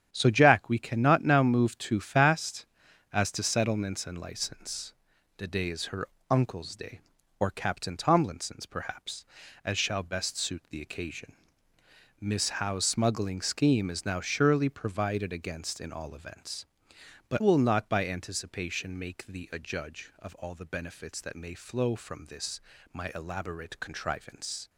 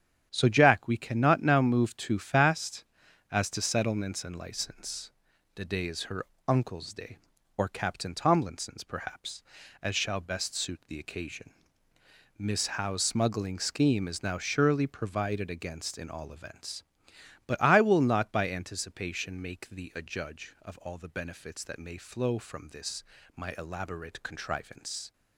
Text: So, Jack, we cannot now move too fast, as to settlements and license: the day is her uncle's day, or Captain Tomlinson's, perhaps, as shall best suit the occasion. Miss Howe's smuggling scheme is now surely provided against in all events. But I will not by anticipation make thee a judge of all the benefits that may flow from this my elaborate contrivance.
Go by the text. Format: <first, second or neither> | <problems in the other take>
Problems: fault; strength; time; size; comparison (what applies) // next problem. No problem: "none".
second | starts louder than the rest; strong; until 1.1 s; 9 dB; strong in the second // pauses between "her" and "uncle's"; slight; at 6.0 s; 0.24 s long; slight in the second // skips "I"; at 17.4 s // pauses between "this" and "my"; slight; at 22.6 s; 0.32 s long; slight in the second